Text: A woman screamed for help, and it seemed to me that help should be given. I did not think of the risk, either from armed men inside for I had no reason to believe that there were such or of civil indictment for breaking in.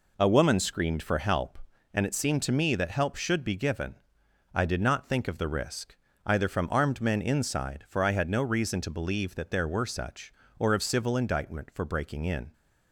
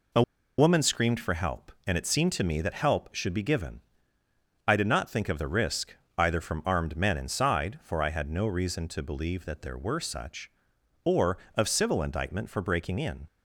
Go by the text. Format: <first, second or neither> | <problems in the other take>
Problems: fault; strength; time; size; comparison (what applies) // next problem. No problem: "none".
first | pauses between "A" and "woman"; slight; at 0.2 s; 0.36 s long